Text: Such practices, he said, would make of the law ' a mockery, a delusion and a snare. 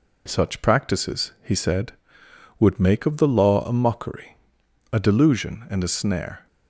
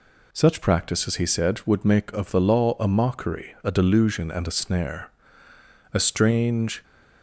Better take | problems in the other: first | goes on to say "A strange"; noticeable; from 5.9 s on; 0.88 s long

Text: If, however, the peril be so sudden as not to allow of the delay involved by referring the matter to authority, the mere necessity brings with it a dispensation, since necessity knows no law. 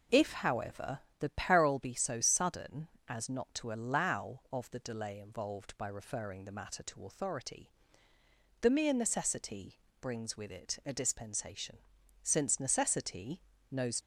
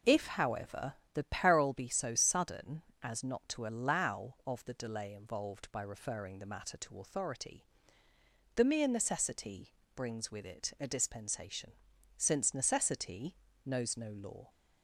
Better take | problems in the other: second | pauses between "necessity" and "brings"; slight; at 9.7 s; 0.26 s long; slight in the second // pauses between "necessity" and "knows"; slight; at 13.4 s; 0.30 s long; slight in the second // stops before "no law"; at 14.0 s

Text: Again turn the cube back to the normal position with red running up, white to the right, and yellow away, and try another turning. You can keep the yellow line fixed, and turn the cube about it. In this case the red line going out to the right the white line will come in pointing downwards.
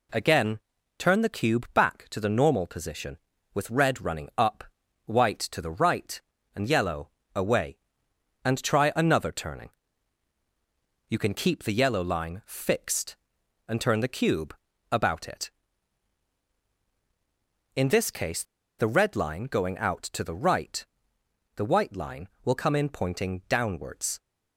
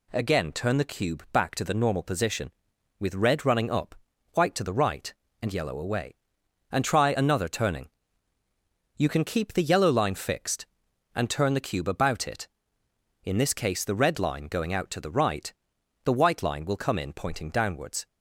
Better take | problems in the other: second | pauses between "Again" and "turn"; at 0.5 s; 0.40 s long // pauses between "yellow" and "away"; slight; at 7.0 s; 0.26 s long // pauses between "cube" and "about"; slight; at 14.5 s; 0.36 s long // pauses between "case" and "the"; at 18.4 s; 0.36 s long // pauses between "right" and "the"; noticeable; at 20.8 s; 0.70 s long; noticeable in the second

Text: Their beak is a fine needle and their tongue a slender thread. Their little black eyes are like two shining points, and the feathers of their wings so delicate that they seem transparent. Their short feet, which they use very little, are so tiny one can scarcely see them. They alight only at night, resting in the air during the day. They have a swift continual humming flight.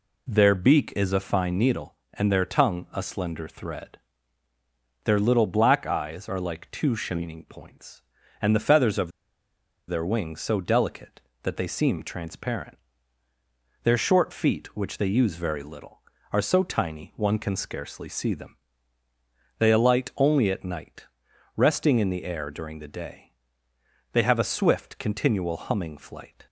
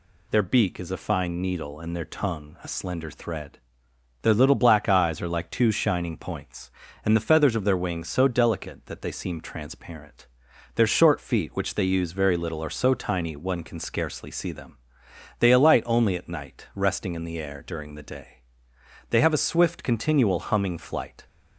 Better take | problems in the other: second | pauses between "of" and "their"; noticeable; at 9.1 s; 0.77 s long

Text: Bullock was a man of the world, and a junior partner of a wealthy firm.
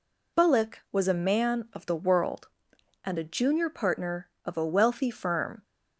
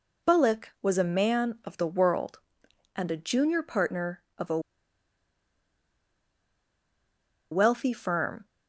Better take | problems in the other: first | pauses between "a" and "wealthy"; strong; at 4.5 s; 2.9 s long

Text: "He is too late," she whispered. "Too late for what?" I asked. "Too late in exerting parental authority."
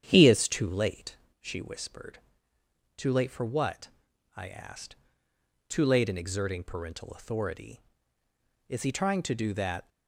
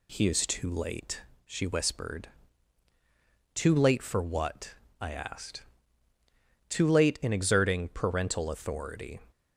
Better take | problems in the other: second | starts louder than the rest; strong; until 1.0 s; 9 dB // goes on to say "Is he trying to do that"; noticeable; from 8.6 s on; 1.2 s long

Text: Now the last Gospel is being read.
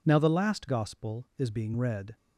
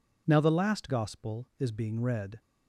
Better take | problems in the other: neither | none

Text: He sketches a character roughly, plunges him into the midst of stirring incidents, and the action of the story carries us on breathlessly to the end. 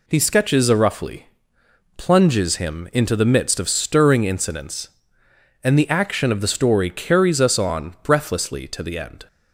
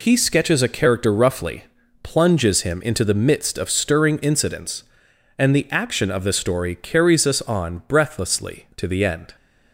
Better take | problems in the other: second | skips "character"; at 0.7 s

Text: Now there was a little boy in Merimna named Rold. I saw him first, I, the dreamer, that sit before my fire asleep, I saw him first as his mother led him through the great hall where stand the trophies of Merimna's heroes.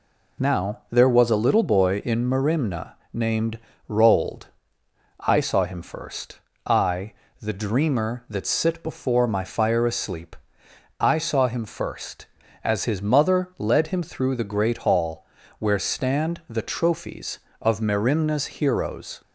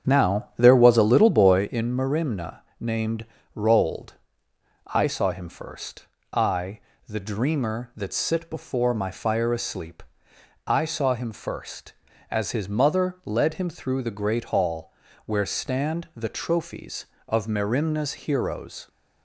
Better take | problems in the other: first | starts louder than the rest; strong; until 1.7 s; 8 dB // pauses between "Merimna" and "named"; slight; at 2.5 s; 0.20 s long; slight in the first // pauses between "named" and "Rold"; slight; at 3.2 s; 0.30 s long; slight in the first // pauses between "hall" and "where"; slight; at 14.9 s; 0.34 s long; slight in the first

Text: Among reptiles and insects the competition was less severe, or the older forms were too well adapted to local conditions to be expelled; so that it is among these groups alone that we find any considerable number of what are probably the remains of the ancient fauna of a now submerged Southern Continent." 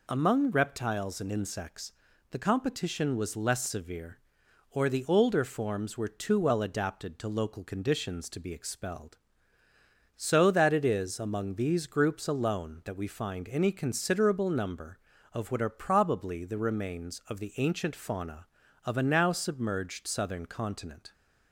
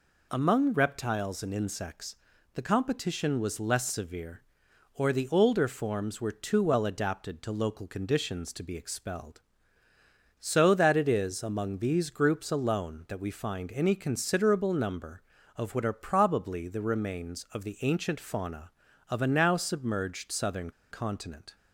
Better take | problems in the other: first | pauses between "insects" and "the"; at 2.1 s; 0.40 s long; also in the first // pauses between "Southern" and "Continent"; slight; at 20.7 s; 0.20 s long

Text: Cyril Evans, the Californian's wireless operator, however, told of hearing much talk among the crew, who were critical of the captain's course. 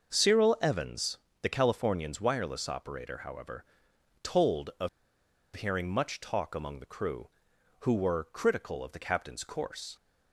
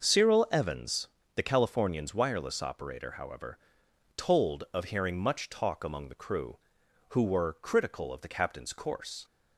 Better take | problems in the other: second | starts louder than the rest; noticeable; until 1.1 s; 6 dB; noticeable in the second // pauses between "of" and "hearing"; noticeable; at 4.8 s; 0.66 s long

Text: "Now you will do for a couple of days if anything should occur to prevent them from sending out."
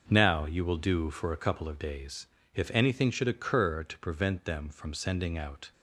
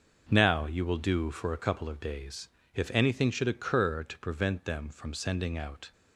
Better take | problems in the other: neither | starts louder than the rest; the same in both // pauses between "days" and "if"; slight; the same in both

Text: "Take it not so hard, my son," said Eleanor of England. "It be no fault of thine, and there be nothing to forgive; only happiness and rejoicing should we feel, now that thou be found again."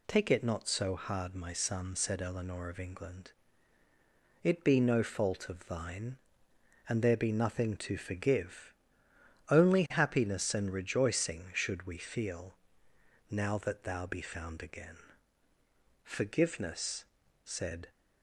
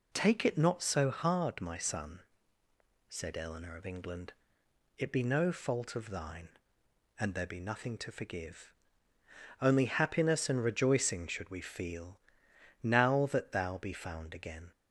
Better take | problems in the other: second | goes on to say "Forgiveness said"; strong; from 16.0 s on; 1.8 s long

